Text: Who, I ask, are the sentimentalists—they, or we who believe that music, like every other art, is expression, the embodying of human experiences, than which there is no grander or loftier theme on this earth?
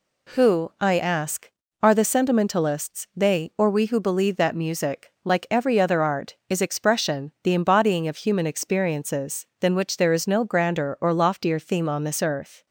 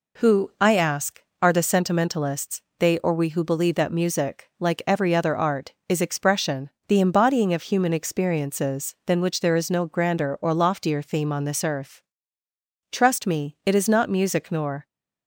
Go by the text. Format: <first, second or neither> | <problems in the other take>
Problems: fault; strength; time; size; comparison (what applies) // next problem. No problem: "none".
first | goes on to say "Trust me it is not music nor"; strong; from 12.9 s on; 1.9 s long